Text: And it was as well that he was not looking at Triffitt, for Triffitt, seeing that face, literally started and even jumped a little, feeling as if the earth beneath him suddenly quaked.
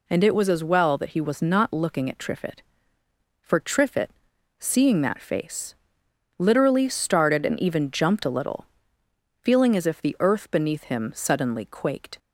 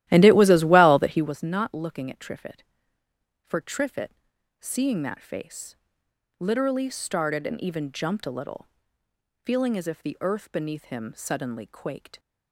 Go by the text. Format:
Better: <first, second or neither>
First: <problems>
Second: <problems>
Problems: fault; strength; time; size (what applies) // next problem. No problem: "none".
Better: first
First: none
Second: starts louder than the rest; strong; until 1.4 s; 14 dB